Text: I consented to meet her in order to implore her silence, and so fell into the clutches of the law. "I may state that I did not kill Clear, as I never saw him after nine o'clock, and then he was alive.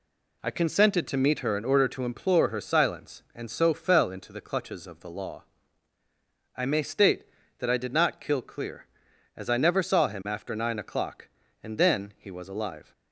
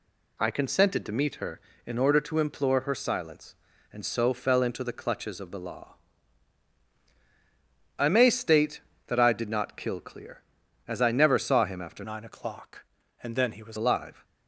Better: first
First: none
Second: changes voice from "nine" to "was"; from 12.0 to 13.7 s; 1.7 s long

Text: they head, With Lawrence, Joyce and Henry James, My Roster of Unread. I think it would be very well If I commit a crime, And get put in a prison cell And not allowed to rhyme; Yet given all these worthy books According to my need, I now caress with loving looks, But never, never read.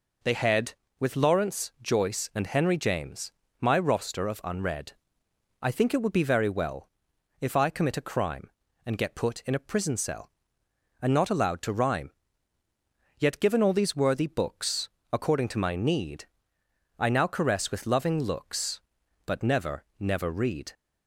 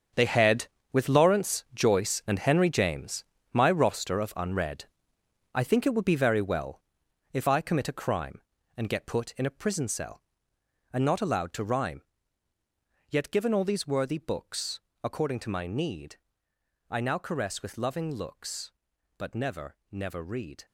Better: first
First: pauses between "well" and "If"; noticeable; at 6.8 s; 0.52 s long // pauses between "books" and "According"; slight; at 14.8 s; 0.24 s long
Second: gets quieter; strong; throughout; 12 dB // pauses between "well" and "If"; noticeable; at 6.8 s; 0.52 s long // pauses between "books" and "According"; slight; at 14.7 s; 0.24 s long

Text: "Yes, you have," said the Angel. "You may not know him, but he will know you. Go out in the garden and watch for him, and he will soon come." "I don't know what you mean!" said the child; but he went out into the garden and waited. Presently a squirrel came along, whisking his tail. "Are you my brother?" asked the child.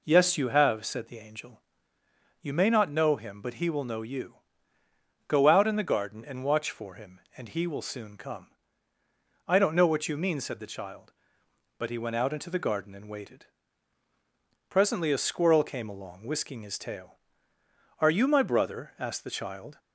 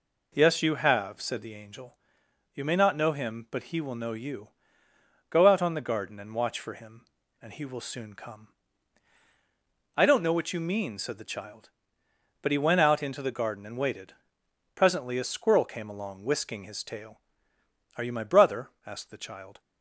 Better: first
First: none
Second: says "on" for "in"; at 5.6 s

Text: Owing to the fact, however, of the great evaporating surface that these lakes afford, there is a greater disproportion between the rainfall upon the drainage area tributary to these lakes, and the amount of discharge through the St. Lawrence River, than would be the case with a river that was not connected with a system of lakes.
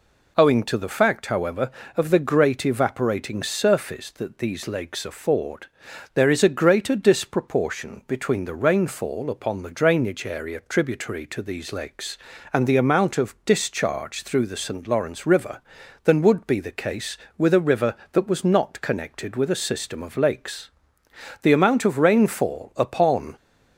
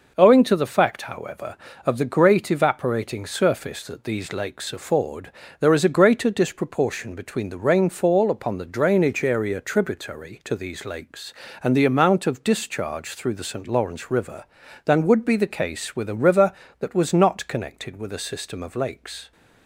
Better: second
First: goes on to say "The amount of rainfall upon"; strong; from 21.4 s on; 1.9 s long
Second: none

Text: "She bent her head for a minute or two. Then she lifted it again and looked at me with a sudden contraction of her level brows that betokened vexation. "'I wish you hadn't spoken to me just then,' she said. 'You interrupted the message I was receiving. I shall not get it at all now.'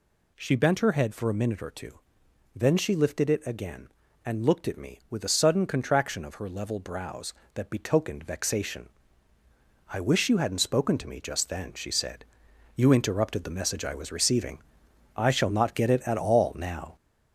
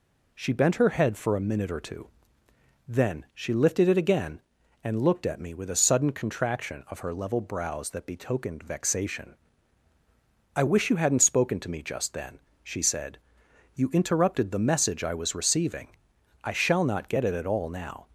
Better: second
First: gets louder; noticeable; throughout; 4.5 dB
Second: none

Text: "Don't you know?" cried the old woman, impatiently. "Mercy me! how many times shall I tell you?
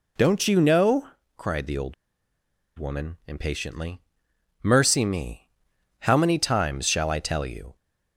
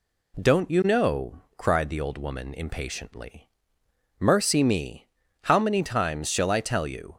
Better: second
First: pauses between "old" and "woman"; noticeable; at 1.9 s; 0.84 s long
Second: none

